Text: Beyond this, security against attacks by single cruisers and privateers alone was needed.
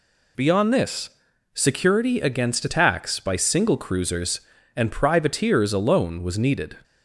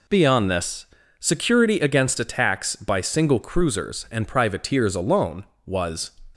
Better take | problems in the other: first | stops before "needed"; at 6.3 s

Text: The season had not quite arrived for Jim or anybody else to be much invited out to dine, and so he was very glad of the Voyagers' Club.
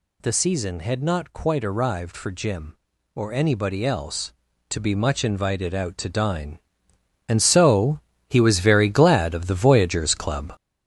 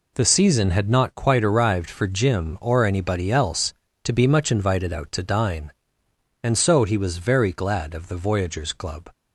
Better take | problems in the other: second | gets louder; strong; throughout; 7.5 dB // pauses between "so" and "he"; slight; at 7.9 s; 0.30 s long

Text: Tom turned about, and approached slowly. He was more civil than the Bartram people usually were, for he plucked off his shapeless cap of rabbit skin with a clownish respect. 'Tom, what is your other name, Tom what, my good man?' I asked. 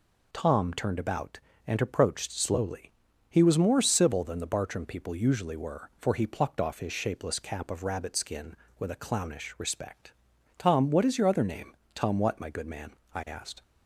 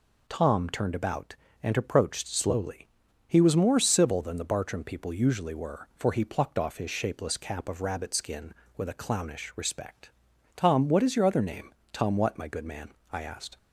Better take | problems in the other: neither | none

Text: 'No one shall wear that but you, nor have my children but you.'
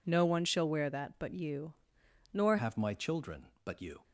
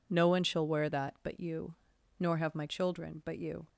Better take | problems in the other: second | changes voice at "have"; from 2.5 s on; 1.5 s long

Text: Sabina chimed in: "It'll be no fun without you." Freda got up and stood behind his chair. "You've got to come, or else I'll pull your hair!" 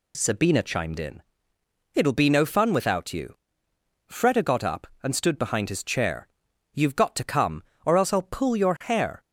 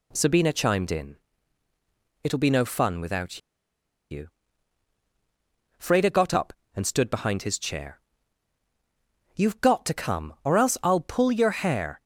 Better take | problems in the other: first | pauses between "without" and "you"; noticeable; at 3.3 s; 0.71 s long

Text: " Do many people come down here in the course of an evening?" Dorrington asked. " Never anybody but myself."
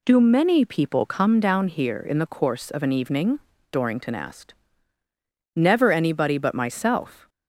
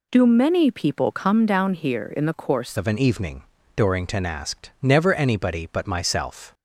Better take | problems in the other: first | changes voice at "of"; from 2.7 s on; 3.8 s long

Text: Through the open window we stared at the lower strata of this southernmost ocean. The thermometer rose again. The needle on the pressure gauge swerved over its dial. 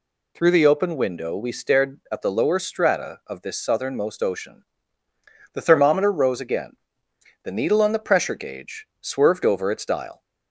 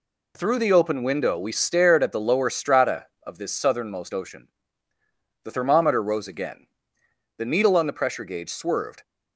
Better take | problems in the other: first | stops before "over its dial"; at 9.0 s

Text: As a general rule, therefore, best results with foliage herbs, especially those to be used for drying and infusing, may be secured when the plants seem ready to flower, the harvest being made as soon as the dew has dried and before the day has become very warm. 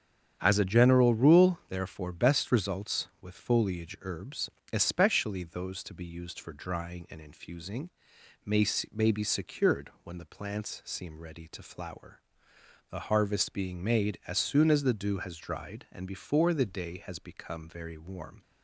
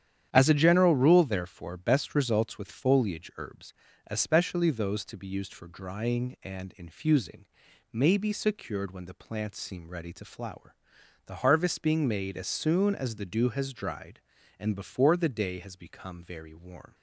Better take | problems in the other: second | starts louder than the rest; strong; until 1.4 s; 8 dB; strong in the second // says "may" twice; at 8.9 s

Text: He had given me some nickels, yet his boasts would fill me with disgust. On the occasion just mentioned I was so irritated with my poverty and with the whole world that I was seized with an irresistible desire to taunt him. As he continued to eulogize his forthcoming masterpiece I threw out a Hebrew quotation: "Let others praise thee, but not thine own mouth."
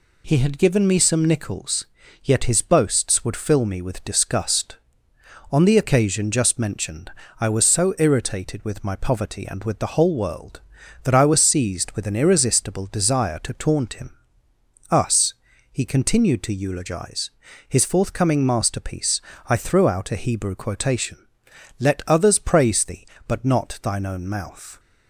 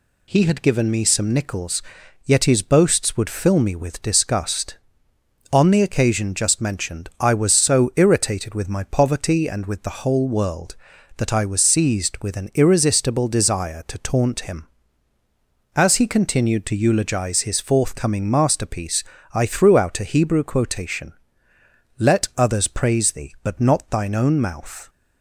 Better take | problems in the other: second | pauses between "mentioned" and "I"; slight; at 7.1 s; 0.28 s long // says "Us" for "As"; at 14.8 s // pauses between "eulogize" and "his"; at 17.2 s; 0.38 s long // pauses between "masterpiece" and "I"; slight; at 19.2 s; 0.26 s long; slight in the second

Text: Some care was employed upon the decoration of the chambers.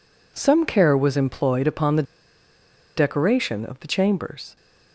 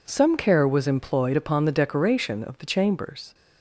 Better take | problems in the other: second | pauses between "the" and "decoration"; noticeable; at 2.0 s; 0.93 s long

